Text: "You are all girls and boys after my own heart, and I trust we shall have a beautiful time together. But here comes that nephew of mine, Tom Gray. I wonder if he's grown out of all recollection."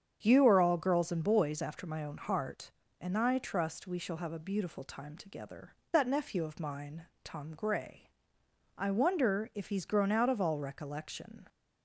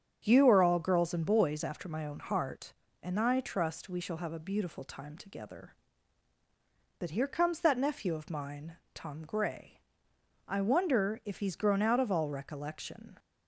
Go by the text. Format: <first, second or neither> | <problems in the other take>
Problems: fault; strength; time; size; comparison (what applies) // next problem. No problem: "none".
second | starts louder than the rest; strong; until 1.2 s; 7.5 dB; strong in the second // skips "But here comes"; at 5.8 s